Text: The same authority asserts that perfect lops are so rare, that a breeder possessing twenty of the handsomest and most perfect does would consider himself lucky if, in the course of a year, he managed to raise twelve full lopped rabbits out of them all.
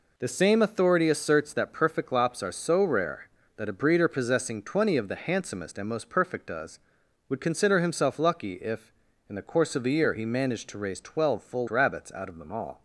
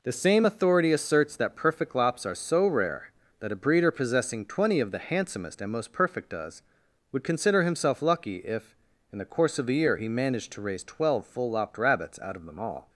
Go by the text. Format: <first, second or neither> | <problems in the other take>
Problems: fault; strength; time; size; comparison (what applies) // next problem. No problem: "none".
second | skips "lopped"; at 11.6 s